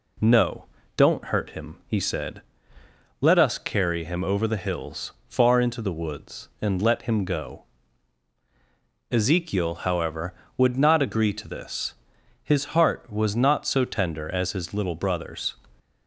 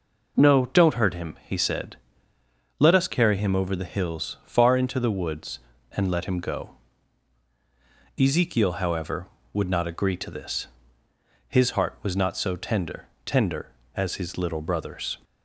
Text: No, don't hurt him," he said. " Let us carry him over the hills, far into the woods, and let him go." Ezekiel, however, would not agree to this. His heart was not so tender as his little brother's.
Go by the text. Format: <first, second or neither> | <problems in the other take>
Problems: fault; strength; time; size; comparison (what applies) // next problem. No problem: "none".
first | says "tender" twice; at 13.2 s